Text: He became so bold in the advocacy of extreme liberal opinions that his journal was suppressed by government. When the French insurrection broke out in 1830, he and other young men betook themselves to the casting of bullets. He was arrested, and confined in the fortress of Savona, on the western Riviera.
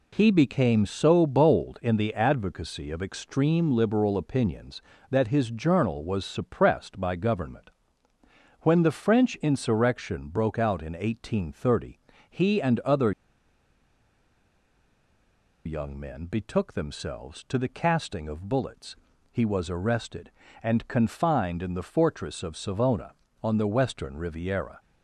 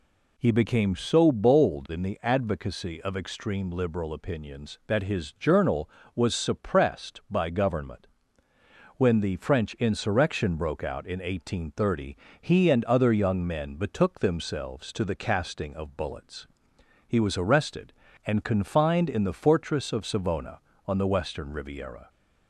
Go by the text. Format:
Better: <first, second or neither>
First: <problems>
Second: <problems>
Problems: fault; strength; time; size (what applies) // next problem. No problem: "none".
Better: second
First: pauses between "other" and "young"; strong; at 13.1 s; 2.5 s long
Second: none